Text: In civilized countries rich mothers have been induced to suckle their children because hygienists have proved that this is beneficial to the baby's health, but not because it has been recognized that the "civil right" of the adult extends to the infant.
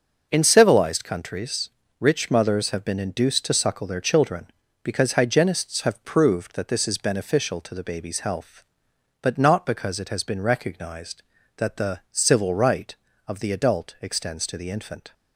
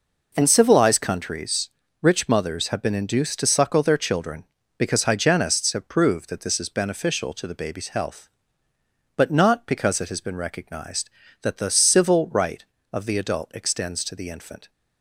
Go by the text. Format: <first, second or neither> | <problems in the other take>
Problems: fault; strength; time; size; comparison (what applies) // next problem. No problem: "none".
neither | pauses between "countries" and "rich"; slight; the same in both